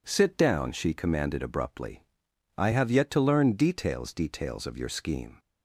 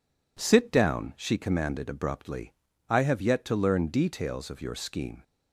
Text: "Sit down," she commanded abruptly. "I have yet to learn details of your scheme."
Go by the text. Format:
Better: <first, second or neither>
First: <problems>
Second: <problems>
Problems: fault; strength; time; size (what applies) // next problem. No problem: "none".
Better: second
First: says "details" twice; at 4.1 s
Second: none